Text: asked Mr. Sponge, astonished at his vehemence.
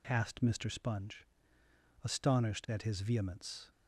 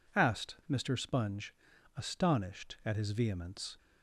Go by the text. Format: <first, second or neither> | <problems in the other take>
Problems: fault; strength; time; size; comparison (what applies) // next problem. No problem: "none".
neither | none